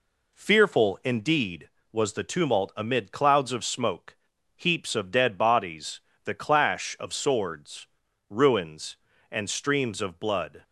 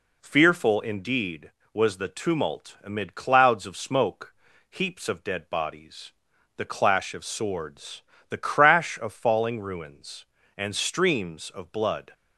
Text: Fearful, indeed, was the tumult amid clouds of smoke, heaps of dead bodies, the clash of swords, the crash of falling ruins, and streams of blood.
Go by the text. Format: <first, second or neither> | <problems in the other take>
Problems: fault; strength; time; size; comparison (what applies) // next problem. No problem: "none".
second | skips "the crash of falling"; at 8.0 s